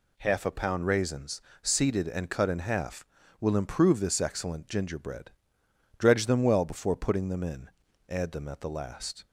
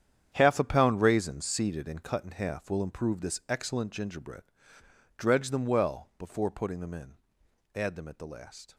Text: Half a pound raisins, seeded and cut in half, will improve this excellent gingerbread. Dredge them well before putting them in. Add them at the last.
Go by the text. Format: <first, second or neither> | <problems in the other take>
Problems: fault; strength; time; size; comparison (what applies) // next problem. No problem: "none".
first | gets quieter; strong; throughout; 12.5 dB